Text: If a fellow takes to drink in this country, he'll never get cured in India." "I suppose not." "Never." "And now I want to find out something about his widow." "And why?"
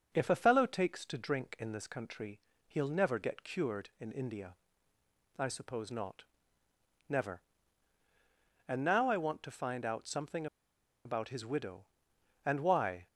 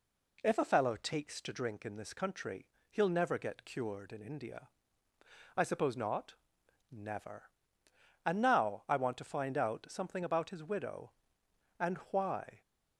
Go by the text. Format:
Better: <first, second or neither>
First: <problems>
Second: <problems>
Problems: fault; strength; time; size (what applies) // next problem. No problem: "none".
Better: second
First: starts louder than the rest; until 1.1 s; 6.5 dB // pauses between "something" and "about"; noticeable; at 10.4 s; 0.59 s long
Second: none